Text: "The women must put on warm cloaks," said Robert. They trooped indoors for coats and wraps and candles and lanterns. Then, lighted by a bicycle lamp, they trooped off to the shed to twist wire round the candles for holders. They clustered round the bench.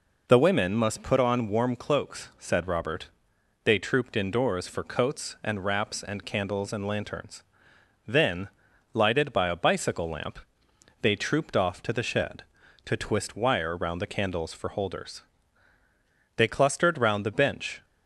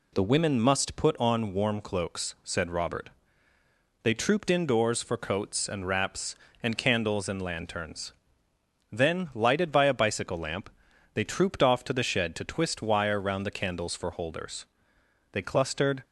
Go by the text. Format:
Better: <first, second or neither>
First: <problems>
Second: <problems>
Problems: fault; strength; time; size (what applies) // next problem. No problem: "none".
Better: first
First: none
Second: stops before "round the bench"; at 16.0 s